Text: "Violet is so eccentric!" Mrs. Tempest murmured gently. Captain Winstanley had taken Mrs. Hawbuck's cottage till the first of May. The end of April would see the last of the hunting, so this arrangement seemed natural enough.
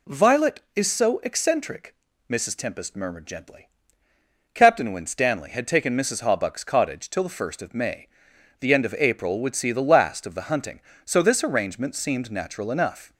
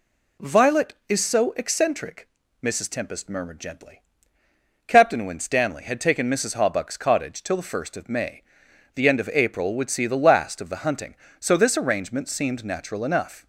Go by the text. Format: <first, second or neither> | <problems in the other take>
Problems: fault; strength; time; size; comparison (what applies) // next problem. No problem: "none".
neither | none